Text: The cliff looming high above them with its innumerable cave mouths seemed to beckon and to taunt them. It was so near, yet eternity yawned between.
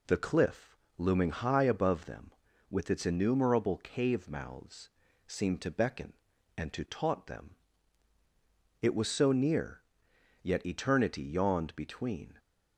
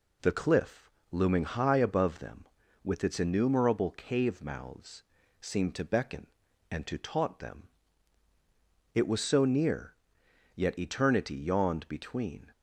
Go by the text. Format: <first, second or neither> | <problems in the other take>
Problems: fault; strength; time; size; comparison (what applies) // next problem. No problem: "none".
neither | pauses between "cliff" and "looming"; slight; the same in both // pauses between "mouths" and "seemed"; the same in both